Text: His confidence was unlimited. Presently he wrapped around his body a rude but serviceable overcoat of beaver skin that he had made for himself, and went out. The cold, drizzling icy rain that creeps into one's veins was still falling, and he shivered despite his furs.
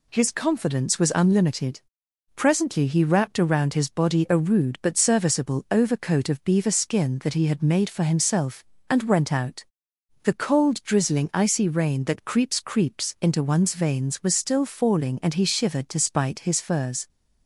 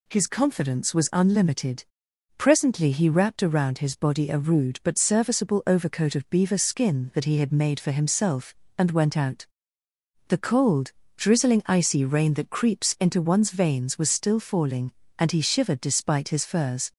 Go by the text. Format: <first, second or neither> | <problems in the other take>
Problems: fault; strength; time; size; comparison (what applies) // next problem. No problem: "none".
second | says "creeps" twice; at 12.6 s